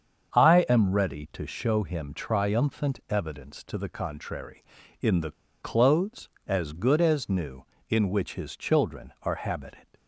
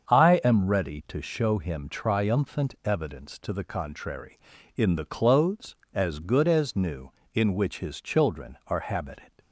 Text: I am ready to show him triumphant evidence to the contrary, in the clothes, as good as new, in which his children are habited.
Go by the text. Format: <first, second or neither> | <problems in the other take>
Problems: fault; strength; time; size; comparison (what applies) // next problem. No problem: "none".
second | starts louder than the rest; until 1.4 s; 7 dB; also in the second // pauses between "the" and "clothes"; slight; at 5.3 s; 0.30 s long